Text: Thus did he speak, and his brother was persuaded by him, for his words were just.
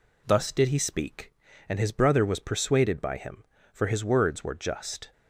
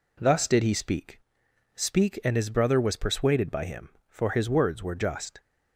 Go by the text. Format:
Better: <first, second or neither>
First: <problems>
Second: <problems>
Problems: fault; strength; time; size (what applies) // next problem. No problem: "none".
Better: first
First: none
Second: says "speak" twice; at 1.7 s